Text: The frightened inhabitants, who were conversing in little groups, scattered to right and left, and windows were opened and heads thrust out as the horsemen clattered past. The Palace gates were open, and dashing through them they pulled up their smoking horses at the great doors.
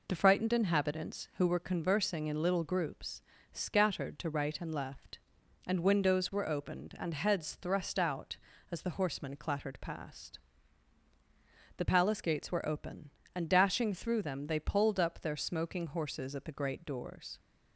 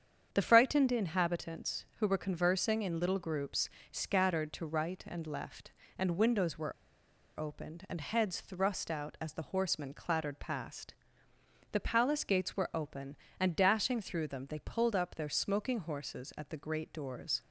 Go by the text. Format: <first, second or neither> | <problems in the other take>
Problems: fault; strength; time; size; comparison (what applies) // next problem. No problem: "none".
first | starts louder than the rest; strong; until 1.3 s; 8 dB // pauses between "were" and "opened"; noticeable; at 6.7 s; 0.66 s long